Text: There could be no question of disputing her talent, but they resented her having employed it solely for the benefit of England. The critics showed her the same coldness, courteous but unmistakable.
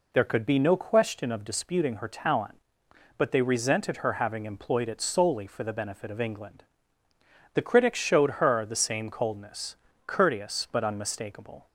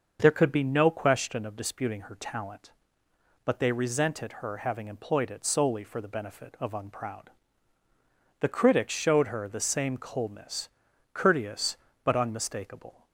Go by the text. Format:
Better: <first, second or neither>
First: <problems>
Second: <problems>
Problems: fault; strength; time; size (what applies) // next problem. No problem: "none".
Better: first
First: none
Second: starts louder than the rest; noticeable; until 1.2 s; 6 dB // says "Unproud" for "England"; at 6.7 s